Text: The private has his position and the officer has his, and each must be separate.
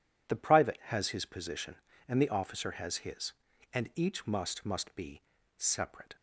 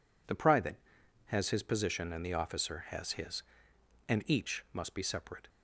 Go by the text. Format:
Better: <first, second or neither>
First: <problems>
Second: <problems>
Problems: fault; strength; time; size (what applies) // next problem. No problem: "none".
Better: second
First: says "must" twice; at 4.6 s // pauses between "be" and "separate"; slight; at 5.2 s; 0.36 s long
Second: none